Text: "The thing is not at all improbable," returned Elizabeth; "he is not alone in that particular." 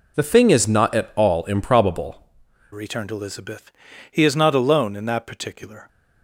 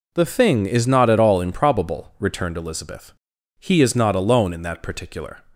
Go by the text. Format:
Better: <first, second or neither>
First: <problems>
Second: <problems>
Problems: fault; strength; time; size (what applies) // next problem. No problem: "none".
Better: second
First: changes voice at "returned"; from 2.7 s on; 3.1 s long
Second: none